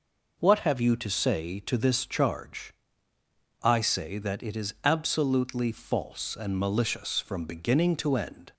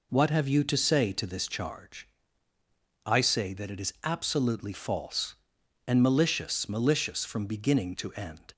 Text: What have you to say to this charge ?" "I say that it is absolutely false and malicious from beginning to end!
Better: first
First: none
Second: says "malicious" twice; at 6.6 s

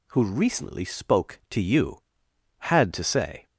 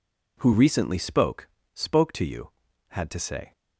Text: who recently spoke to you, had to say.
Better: first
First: none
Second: says "spoke" twice; at 1.7 s

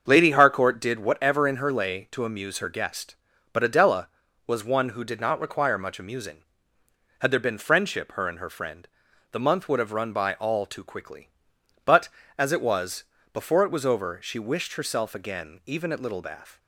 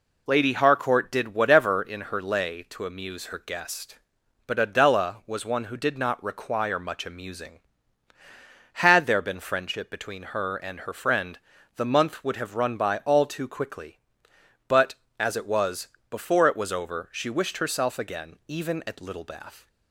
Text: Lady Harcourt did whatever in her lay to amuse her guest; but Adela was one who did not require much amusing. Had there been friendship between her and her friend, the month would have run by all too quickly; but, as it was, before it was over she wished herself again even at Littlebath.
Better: second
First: starts louder than the rest; until 1.1 s; 7 dB // skips "between"; at 8.1 s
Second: none

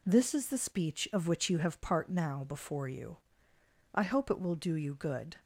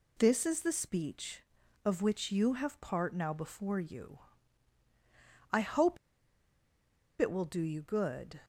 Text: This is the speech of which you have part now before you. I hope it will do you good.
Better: first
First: none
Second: pauses between "hope" and "it"; at 5.9 s; 1.2 s long

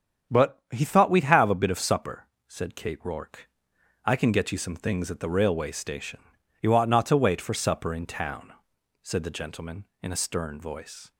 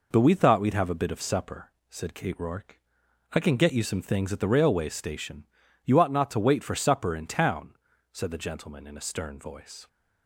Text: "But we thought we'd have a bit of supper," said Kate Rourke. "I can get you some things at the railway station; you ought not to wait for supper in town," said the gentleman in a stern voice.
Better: second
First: starts louder than the rest; strong; until 1.3 s; 7.5 dB // says "he" for "we"; at 0.7 s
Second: none

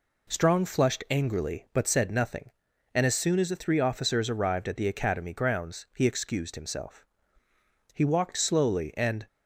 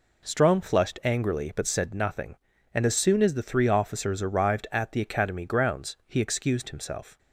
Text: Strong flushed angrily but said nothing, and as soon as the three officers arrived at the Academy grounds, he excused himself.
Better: second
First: goes on to say "He walked slowly and"; from 7.9 s on; 1.3 s long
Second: none

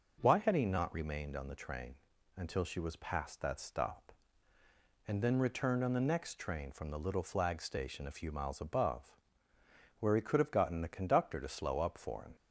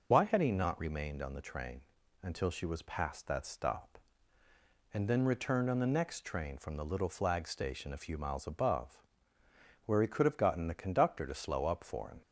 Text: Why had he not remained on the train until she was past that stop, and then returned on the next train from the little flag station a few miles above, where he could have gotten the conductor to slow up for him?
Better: first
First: pauses between "train" and "until"; at 1.9 s; 0.40 s long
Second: loses the start of "Why"; at 0.1 s; 60 ms // pauses between "train" and "until"; at 1.8 s; 0.40 s long

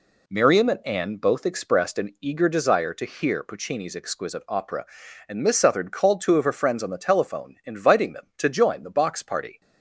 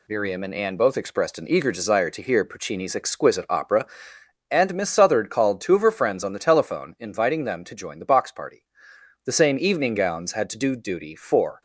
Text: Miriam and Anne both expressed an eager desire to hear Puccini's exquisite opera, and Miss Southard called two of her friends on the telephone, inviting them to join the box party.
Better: first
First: none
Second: goes on to say "The same evening gowns had to do duty for"; strong; from 9.2 s on; 2.3 s long

